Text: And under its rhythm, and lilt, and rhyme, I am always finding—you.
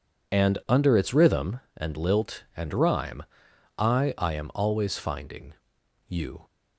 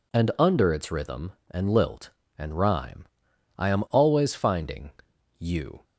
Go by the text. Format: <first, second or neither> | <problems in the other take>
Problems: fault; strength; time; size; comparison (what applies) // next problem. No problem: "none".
second | says "I" twice; at 4.1 s